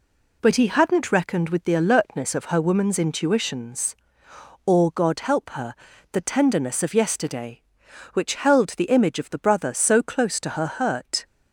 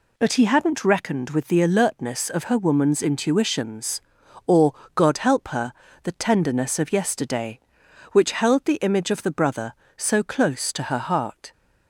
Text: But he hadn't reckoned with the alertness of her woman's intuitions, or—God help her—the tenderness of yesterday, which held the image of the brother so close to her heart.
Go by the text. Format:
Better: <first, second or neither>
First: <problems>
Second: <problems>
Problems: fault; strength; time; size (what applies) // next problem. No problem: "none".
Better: second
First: says "hurt" for "heart"; at 10.6 s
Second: none